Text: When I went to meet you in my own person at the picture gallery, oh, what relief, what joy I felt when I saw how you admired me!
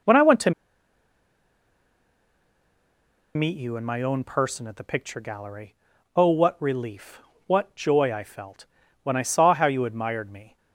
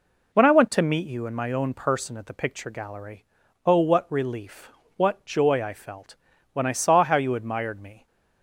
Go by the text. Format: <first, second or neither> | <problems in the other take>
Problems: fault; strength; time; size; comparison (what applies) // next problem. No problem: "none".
second | pauses between "to" and "meet"; strong; at 0.5 s; 2.8 s long // pauses between "felt" and "when"; slight; at 8.6 s; 0.36 s long; slight in the second